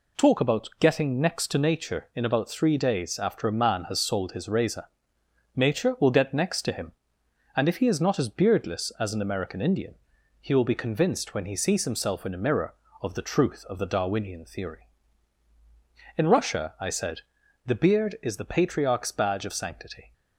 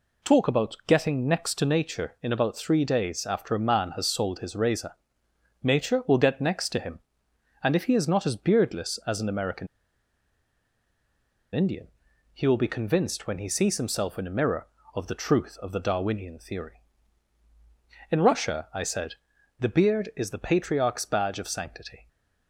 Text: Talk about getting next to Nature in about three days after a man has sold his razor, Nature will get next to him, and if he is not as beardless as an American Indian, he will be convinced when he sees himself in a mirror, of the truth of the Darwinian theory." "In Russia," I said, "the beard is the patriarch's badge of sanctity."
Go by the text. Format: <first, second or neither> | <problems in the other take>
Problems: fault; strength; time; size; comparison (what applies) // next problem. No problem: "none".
first | pauses between "American" and "Indian"; strong; at 9.6 s; 1.8 s long